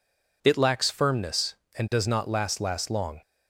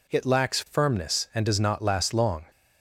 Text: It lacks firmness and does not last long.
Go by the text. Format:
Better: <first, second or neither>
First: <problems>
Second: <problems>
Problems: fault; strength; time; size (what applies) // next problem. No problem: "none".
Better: second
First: says "last" twice; at 2.5 s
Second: none